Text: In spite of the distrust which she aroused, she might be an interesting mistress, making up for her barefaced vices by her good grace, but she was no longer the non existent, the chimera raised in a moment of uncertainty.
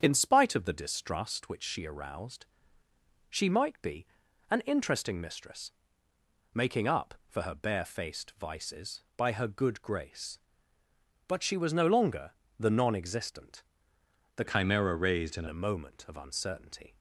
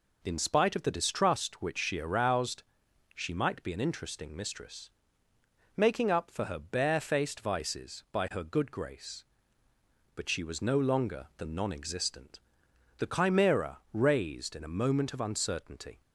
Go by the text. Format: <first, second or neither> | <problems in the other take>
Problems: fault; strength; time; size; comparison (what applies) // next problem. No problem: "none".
second | starts louder than the rest; strong; until 1.0 s; 8 dB // pauses between "be" and "an"; at 4.0 s; 0.42 s long // pauses between "longer" and "the"; slight; at 12.3 s; 0.26 s long // changes voice from "chimera" to "in"; from 14.4 to 15.4 s; 1.0 s long